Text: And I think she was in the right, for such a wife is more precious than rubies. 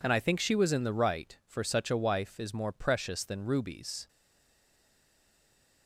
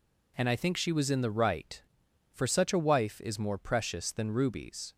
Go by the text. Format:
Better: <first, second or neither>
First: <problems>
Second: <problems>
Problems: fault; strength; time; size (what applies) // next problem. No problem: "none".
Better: second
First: stays silent after the last word; noticeable; from 4.0 s on; 1.8 s long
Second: none